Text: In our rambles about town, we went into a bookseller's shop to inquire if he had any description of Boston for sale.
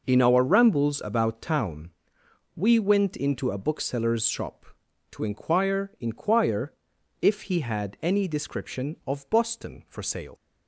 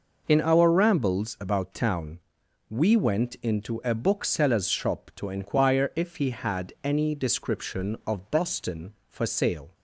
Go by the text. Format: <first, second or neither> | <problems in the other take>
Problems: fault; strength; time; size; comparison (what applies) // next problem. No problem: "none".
second | says "inquire" twice; at 5.9 s